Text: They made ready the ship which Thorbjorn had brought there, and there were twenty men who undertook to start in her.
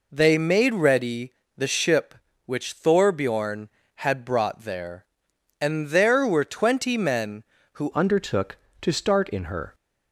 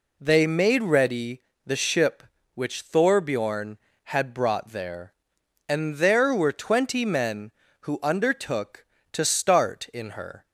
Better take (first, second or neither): second